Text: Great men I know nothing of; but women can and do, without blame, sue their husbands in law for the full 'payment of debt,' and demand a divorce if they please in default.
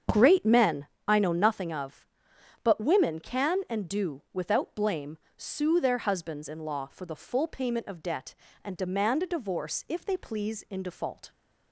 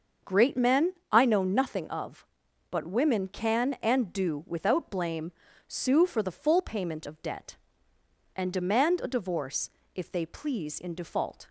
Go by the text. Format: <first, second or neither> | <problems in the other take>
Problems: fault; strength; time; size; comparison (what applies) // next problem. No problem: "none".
first | starts louder than the rest; until 1.4 s; 6.5 dB; strong in the first // pauses between "men" and "I"; slight; at 0.9 s; 0.18 s long; slight in the first // skips "their husbands in law"; at 6.0 s // pauses between "divorce" and "if"; slight; at 9.7 s; 0.26 s long